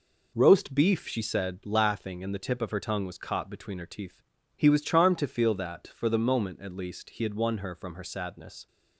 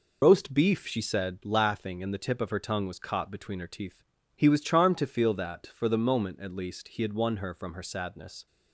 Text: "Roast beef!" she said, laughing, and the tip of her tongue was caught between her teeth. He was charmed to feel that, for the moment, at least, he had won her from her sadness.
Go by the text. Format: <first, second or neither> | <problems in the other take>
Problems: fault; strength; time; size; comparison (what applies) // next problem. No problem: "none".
first | loses the start of "Roast"; at 0.2 s; 75 ms